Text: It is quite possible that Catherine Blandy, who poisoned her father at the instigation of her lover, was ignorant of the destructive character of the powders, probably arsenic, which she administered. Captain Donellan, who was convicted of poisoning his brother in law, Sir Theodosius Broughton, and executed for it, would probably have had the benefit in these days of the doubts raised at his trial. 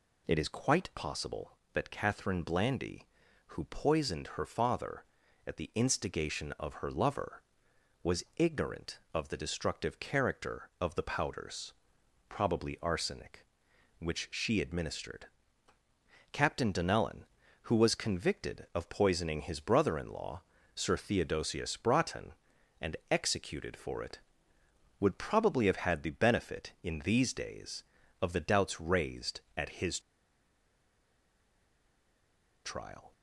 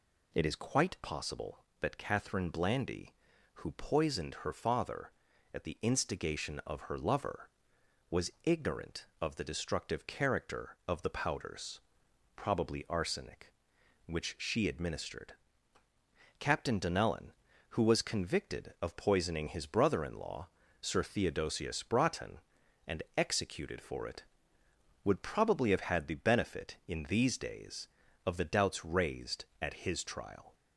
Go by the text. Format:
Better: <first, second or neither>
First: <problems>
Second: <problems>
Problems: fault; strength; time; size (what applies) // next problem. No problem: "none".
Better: second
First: pauses between "and" and "executed"; slight; at 22.9 s; 0.16 s long // pauses between "his" and "trial"; strong; at 29.9 s; 2.6 s long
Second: pauses between "and" and "executed"; slight; at 23.0 s; 0.16 s long